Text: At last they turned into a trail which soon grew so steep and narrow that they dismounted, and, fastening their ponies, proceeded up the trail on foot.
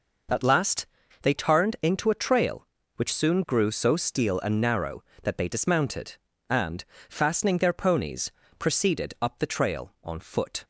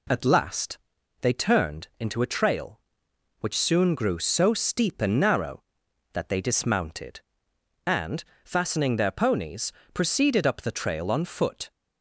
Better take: second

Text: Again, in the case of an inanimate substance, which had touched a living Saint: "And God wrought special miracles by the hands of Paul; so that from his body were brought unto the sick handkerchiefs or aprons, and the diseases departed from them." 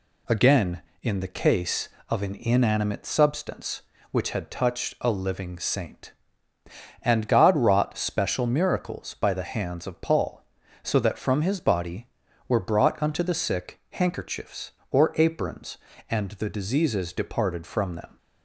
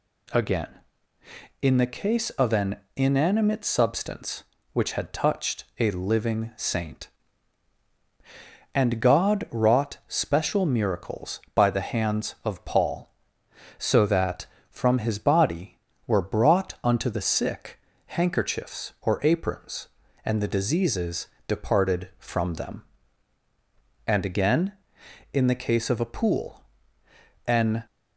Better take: first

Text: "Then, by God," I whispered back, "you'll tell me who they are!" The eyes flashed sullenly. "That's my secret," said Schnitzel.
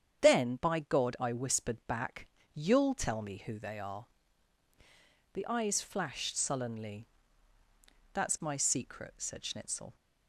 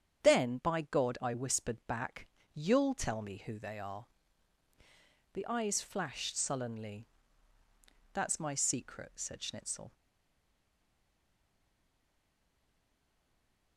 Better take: first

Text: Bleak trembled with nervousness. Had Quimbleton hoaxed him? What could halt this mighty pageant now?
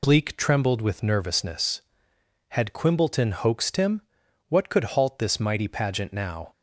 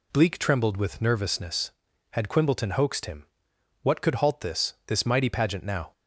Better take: first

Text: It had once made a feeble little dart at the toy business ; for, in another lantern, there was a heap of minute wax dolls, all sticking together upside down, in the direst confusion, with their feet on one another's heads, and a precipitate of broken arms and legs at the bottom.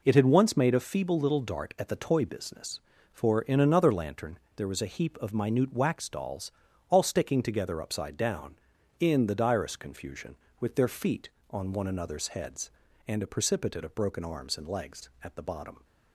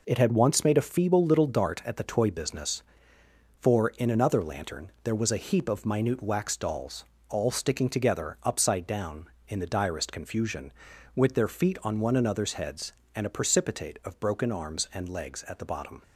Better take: neither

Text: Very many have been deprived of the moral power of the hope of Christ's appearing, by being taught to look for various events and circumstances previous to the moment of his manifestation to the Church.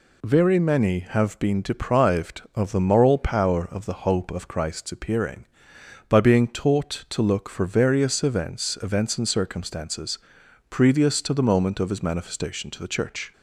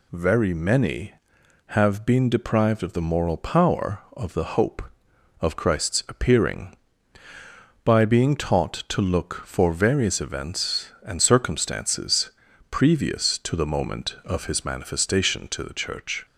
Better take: second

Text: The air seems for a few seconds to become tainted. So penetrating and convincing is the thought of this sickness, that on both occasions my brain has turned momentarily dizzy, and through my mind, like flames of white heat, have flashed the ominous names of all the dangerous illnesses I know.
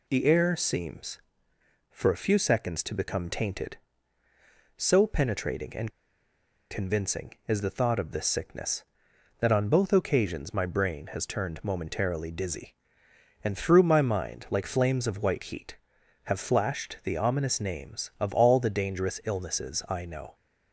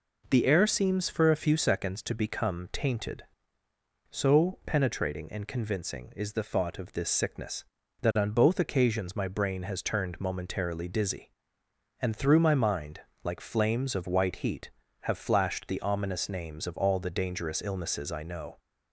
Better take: second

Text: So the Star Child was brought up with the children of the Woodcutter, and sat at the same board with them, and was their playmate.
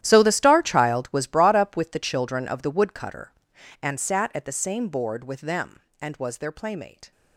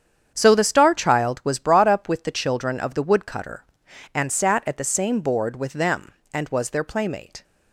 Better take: second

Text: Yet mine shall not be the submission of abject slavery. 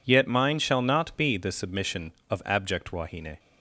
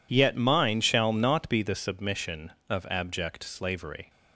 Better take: second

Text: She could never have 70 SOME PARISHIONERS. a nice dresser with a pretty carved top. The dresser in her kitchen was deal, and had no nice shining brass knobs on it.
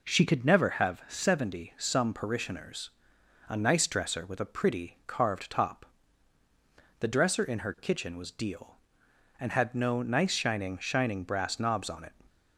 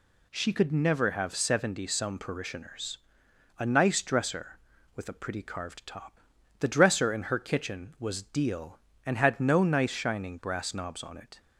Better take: second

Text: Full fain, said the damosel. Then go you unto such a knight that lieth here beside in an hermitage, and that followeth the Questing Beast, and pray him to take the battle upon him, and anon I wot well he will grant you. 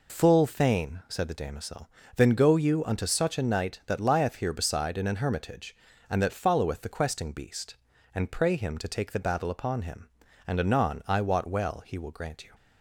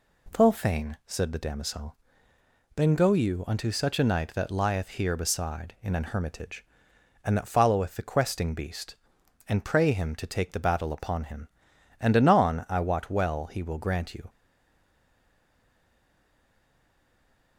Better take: first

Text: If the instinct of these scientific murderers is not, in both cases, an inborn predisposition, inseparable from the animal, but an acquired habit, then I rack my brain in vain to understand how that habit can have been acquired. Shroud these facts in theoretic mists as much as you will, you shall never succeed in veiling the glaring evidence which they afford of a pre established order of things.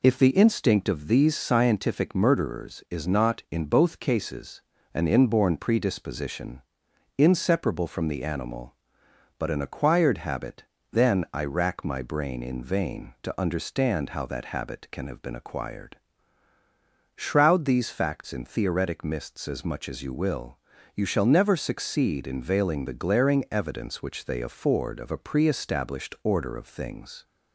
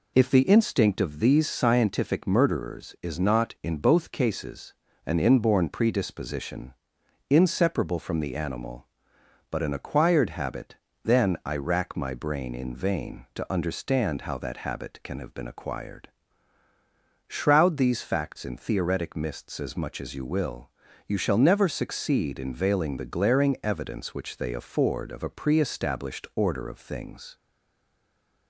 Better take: first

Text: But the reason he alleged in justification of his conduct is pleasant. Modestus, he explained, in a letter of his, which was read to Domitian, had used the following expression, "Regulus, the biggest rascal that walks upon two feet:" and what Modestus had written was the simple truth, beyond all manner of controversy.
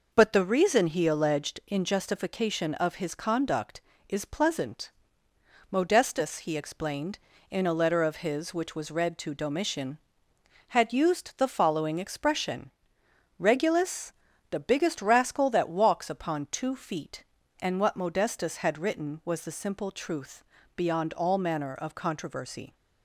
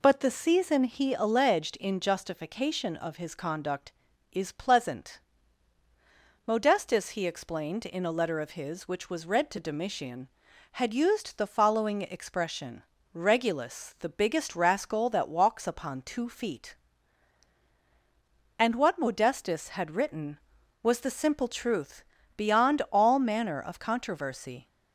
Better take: first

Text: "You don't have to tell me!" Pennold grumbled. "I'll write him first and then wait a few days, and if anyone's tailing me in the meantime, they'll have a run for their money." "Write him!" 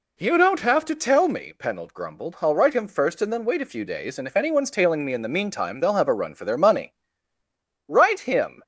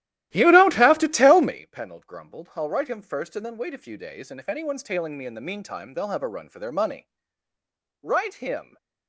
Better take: first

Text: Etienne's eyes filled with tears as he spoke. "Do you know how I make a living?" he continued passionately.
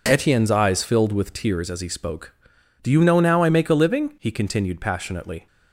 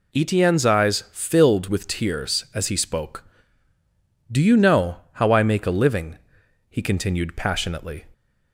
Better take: second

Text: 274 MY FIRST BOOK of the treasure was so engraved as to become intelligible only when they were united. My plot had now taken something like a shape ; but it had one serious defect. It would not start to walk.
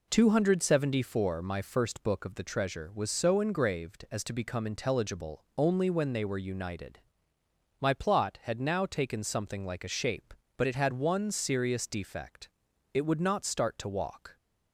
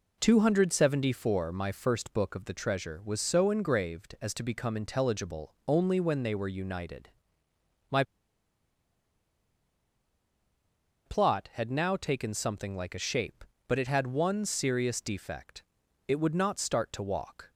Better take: first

